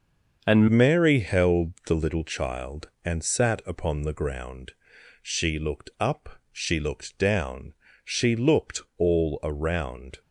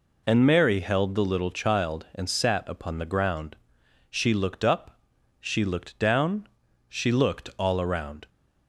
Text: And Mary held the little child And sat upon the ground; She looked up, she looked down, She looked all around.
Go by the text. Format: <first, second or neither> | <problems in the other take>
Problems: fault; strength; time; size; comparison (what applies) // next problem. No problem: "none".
second | starts louder than the rest; until 1.4 s; 6.5 dB // changes voice at "Mary"; from 0.6 s on; 9.6 s long // pauses between "looked" and "all"; slight; at 8.8 s; 0.16 s long